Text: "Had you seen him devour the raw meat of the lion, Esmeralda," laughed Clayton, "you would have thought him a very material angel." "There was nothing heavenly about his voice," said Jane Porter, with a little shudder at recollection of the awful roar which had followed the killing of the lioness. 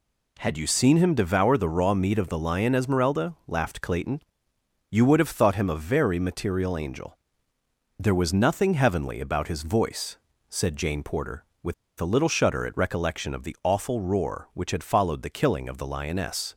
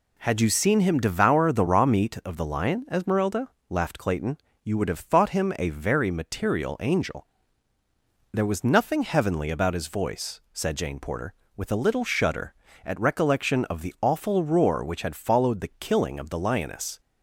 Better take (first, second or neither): second